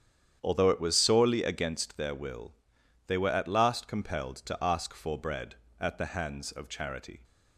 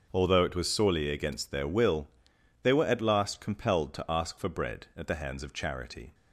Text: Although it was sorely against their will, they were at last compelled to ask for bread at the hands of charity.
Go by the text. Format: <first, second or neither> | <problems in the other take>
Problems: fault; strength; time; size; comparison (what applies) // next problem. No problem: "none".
second | starts louder than the rest; strong; until 1.8 s; 9 dB